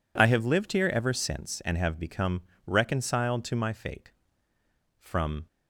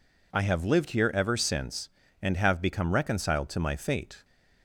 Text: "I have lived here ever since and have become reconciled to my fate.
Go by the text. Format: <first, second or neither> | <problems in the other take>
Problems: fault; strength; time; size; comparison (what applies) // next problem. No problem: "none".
second | pauses between "become" and "reconciled"; slight; at 2.4 s; 0.24 s long // goes on to say "From"; slight; from 4.9 s on; 0.48 s long